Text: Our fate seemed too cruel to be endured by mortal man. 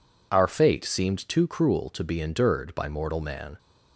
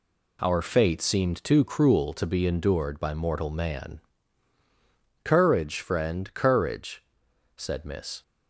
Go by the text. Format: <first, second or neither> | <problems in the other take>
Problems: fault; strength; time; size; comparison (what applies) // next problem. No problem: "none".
first | goes on to say "Courage friend courage said Miss"; strong; from 5.2 s on; 3.0 s long